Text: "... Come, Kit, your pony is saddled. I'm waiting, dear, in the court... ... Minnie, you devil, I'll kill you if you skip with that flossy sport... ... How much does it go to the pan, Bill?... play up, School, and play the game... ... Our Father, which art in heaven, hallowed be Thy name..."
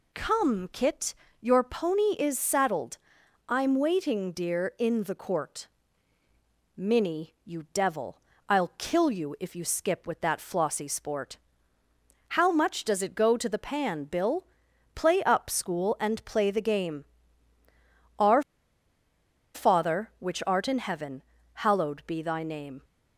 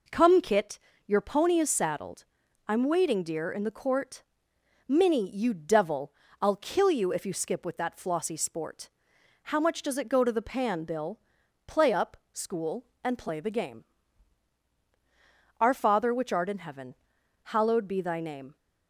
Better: second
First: pauses between "Our" and "Father"; at 18.4 s; 1.1 s long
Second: none

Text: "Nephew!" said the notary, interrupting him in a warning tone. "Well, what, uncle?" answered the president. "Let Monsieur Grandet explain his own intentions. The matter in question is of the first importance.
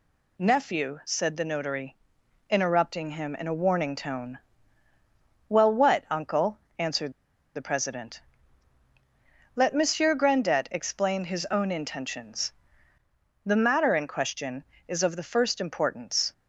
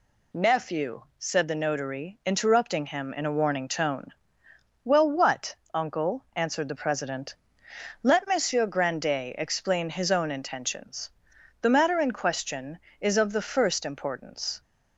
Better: second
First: pauses between "answered" and "the"; at 7.1 s; 0.44 s long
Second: none

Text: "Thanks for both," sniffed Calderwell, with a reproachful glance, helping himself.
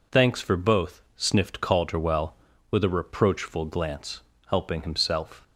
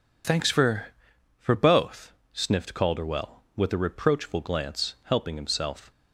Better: first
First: none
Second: says "for" twice; at 1.3 s

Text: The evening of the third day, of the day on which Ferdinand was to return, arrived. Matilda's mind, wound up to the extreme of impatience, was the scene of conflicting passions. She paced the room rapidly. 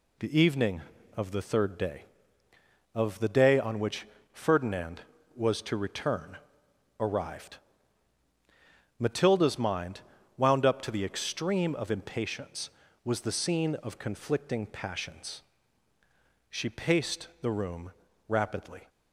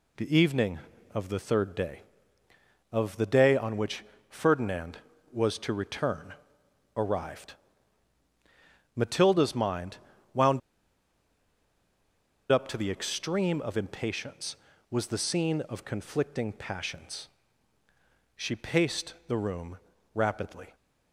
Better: first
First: pauses between "which" and "Ferdinand"; slight; at 4.0 s; 0.24 s long // pauses between "room" and "rapidly"; slight; at 17.9 s; 0.34 s long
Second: pauses between "which" and "Ferdinand"; slight; at 4.0 s; 0.24 s long // pauses between "wound" and "up"; strong; at 10.6 s; 1.9 s long // pauses between "room" and "rapidly"; slight; at 19.7 s; 0.34 s long

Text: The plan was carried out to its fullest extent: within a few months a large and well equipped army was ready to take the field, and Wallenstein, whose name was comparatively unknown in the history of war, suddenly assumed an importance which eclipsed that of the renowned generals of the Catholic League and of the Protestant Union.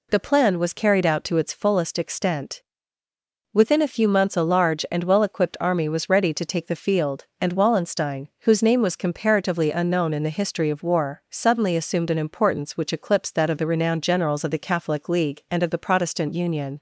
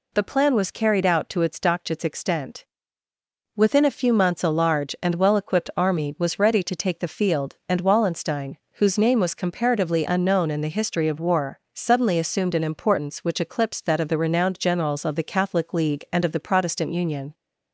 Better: first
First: none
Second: says "dokchits" for "fullest"; at 1.5 s

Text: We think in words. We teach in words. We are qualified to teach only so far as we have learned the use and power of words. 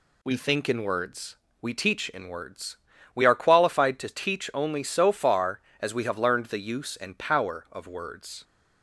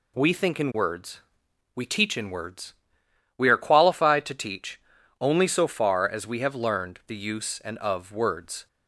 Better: first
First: none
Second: pauses between "teach" and "only"; at 4.8 s; 0.40 s long // skips "power"; at 7.7 s

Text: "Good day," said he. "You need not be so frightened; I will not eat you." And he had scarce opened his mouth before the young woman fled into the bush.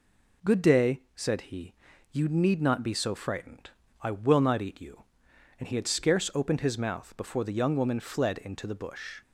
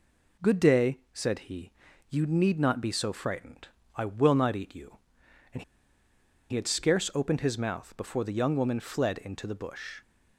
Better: first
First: none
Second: pauses between "And" and "he"; noticeable; at 5.6 s; 0.86 s long

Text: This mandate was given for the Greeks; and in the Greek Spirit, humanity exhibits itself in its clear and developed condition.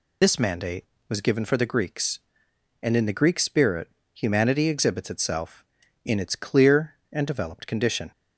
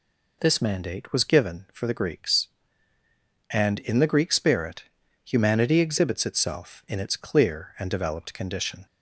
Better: second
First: loses the start of "This"; at 0.2 s; 55 ms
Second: none

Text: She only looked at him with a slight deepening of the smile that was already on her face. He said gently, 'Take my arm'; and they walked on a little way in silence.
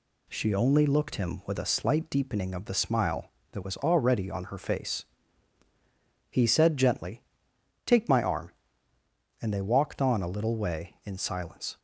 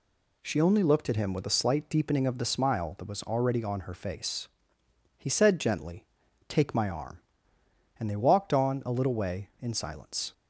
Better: second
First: skips "at"; at 1.1 s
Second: none

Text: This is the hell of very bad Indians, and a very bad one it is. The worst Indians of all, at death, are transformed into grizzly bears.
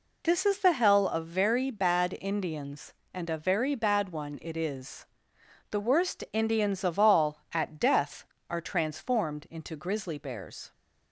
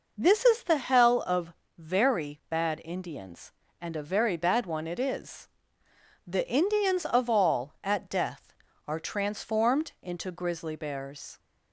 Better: first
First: none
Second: pauses between "of" and "very"; slight; at 1.5 s; 0.24 s long // skips "worst"; at 6.4 s

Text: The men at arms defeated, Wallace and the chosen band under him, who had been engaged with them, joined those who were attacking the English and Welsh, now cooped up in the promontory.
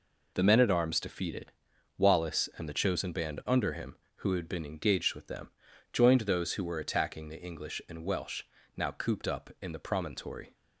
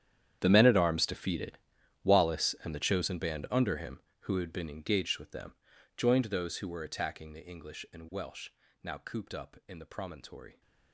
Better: first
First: none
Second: gets quieter; strong; throughout; 18.5 dB

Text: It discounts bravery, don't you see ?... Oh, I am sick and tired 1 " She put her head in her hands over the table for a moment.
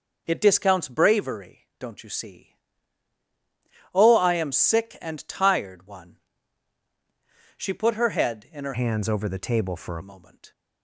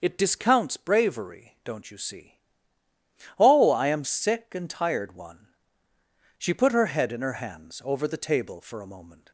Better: second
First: starts louder than the rest; until 1.2 s; 6 dB // changes voice from "hands" to "a"; from 8.7 to 10.0 s; 1.3 s long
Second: starts louder than the rest; until 1.0 s; 6.5 dB

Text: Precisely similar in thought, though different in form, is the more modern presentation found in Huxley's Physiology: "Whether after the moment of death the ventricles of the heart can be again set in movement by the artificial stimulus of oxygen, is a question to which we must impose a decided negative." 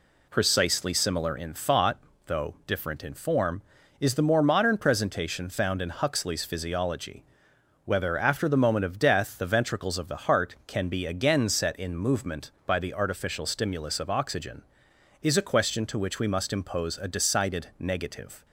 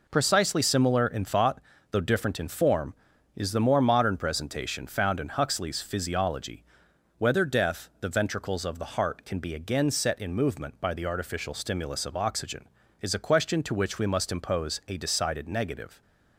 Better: first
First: none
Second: skips "after the moment of"; at 7.4 s

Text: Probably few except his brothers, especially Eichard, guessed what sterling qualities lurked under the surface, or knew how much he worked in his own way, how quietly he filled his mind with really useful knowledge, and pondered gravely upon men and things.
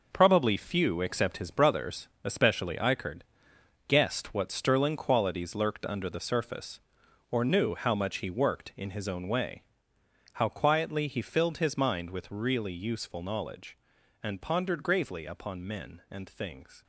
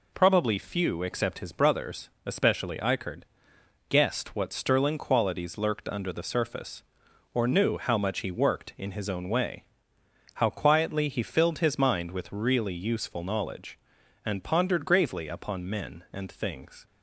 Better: second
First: gets quieter; strong; throughout; 9.5 dB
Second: none

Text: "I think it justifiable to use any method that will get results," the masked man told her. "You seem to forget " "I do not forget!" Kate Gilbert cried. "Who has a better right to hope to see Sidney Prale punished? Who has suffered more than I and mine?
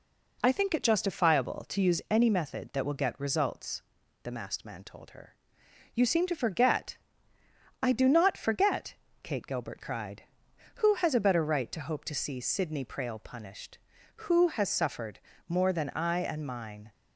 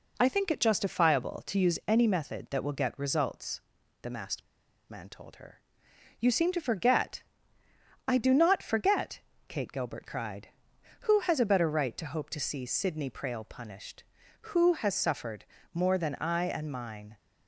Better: first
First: pauses between "suffered" and "more"; slight; at 15.1 s; 0.30 s long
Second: pauses between "masked" and "man"; noticeable; at 4.4 s; 0.48 s long // pauses between "suffered" and "more"; slight; at 15.4 s; 0.30 s long

